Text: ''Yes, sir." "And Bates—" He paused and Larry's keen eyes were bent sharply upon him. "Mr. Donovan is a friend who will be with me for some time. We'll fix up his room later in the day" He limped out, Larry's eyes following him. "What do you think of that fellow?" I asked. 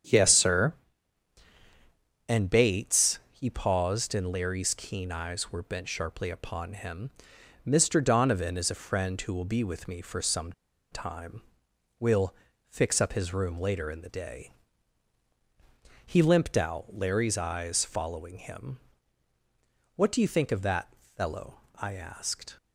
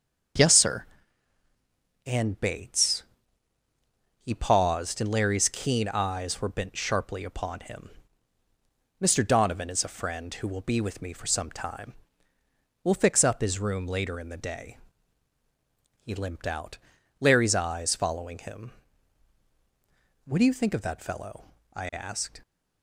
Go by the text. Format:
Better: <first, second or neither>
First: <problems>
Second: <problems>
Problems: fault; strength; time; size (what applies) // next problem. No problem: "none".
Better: second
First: starts louder than the rest; strong; until 2.5 s; 8 dB // pauses between "some" and "time"; at 10.5 s; 0.40 s long // pauses between "We'll" and "fix"; slight; at 12.3 s; 0.34 s long // pauses between "day" and "He"; strong; at 14.5 s; 1.5 s long // pauses between "that" and "fellow"; slight; at 20.9 s; 0.22 s long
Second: starts louder than the rest; until 2.5 s; 7 dB // pauses between "day" and "He"; strong; at 14.7 s; 1.2 s long